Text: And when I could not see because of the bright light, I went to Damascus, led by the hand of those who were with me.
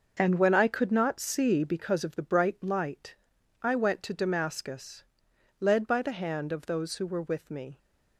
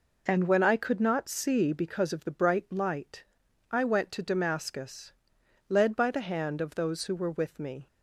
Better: second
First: gets quieter; strong; throughout; 9.5 dB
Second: none

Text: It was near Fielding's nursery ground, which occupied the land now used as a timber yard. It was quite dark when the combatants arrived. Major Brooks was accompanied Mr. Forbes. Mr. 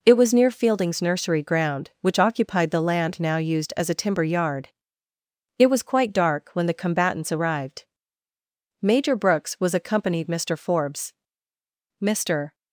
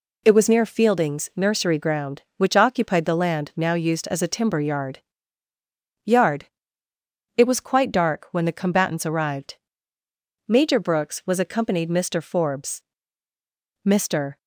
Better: first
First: none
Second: says "yard" twice; at 6.0 s

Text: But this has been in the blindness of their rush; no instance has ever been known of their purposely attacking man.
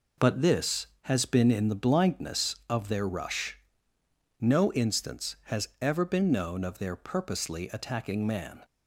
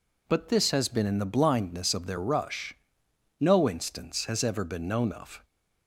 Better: first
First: none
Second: stops before "their purposely attacking man"; at 5.4 s

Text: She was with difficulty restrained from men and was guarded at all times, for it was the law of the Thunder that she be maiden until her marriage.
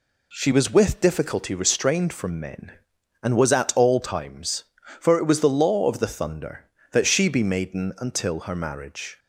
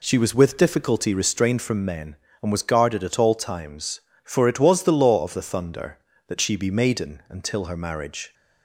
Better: second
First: skips "guarded"; at 3.5 s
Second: none

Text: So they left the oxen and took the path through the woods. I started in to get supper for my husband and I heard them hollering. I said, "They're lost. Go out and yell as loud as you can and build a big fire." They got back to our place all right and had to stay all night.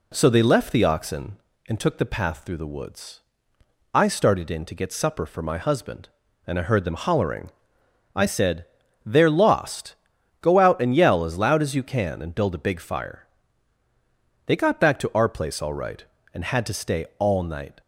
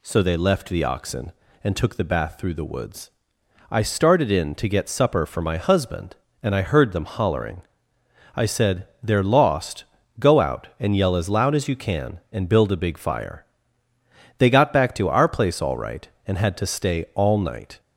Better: first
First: none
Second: says "bath" for "path"; at 2.0 s

